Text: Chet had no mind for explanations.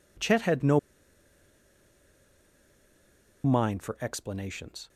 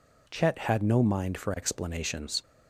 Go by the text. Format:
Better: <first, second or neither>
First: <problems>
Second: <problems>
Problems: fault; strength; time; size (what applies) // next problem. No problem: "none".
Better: second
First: pauses between "no" and "mind"; strong; at 0.7 s; 2.6 s long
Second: none